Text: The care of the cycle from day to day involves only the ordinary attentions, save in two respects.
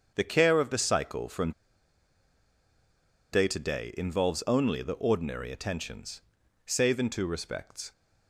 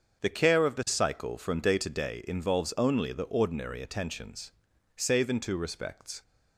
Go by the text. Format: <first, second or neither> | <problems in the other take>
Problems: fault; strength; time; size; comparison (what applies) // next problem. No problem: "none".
second | starts louder than the rest; until 1.1 s; 7 dB; also in the second // pauses between "from" and "day"; strong; at 1.5 s; 1.7 s long